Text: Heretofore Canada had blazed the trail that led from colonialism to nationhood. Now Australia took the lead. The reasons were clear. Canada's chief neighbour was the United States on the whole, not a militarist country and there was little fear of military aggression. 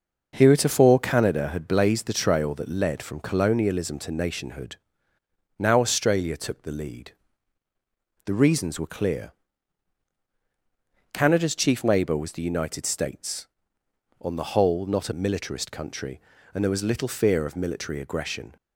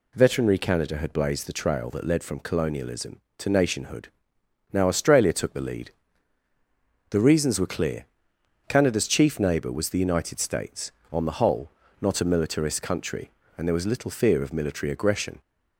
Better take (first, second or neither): first